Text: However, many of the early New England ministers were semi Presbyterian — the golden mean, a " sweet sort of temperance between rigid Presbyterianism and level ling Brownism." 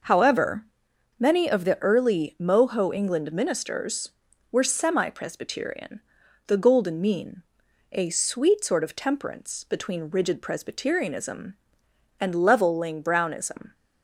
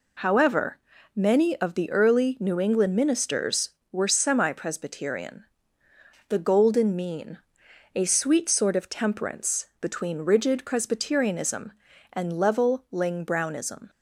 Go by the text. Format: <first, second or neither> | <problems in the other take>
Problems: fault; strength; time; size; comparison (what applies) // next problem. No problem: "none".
second | says "Moho" for "New"; at 2.3 s